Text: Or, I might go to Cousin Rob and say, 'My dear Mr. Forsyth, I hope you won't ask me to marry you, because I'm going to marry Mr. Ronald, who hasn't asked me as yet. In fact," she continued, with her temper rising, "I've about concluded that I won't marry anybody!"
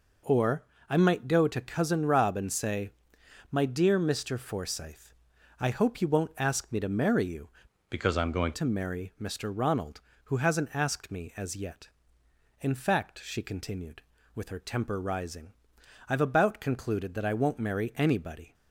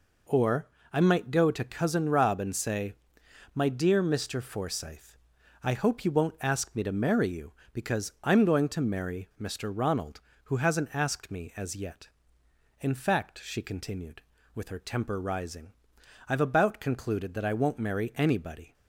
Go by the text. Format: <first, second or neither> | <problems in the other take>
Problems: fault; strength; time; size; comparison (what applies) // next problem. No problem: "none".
second | changes voice from "because" to "going"; from 7.8 to 8.5 s; 0.7 s long